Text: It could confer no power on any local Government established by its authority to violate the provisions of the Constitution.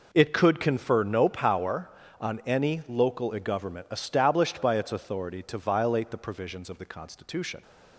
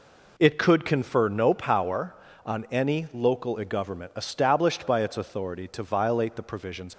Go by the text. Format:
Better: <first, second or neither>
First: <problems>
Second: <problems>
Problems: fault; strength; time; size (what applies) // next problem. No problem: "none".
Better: first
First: none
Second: stops before "of the Constitution"; at 6.9 s